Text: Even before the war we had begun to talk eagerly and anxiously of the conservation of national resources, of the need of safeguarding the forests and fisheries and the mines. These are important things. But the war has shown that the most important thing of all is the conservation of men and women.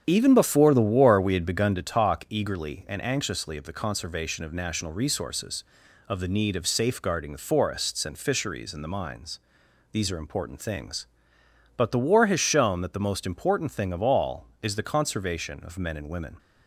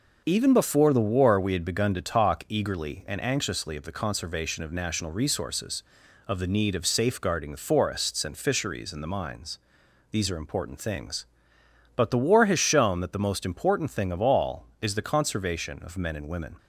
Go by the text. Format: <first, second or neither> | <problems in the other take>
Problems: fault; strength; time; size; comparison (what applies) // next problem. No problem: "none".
second | starts louder than the rest; strong; until 1.9 s; 8 dB